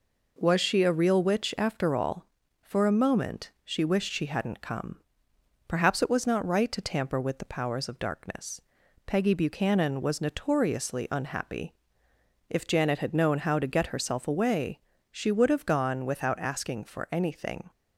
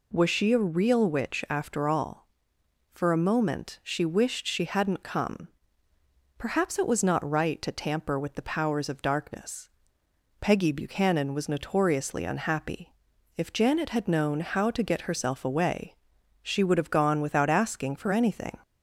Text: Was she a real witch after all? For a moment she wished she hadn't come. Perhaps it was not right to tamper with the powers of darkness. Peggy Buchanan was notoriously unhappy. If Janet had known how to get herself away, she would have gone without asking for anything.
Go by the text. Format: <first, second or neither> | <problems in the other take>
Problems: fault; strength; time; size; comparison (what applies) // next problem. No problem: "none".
neither | none